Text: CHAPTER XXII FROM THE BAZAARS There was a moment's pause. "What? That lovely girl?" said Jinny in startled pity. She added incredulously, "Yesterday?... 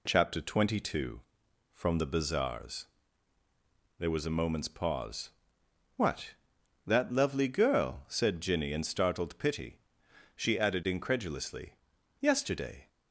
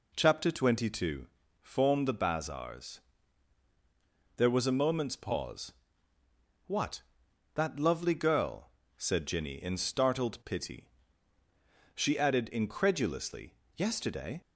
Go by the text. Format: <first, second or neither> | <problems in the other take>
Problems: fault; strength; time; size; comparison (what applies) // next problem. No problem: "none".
first | says "Form" for "FROM"; at 1.5 s // pauses between "BAZAARS" and "There"; strong; at 2.9 s; 1.3 s long; also in the first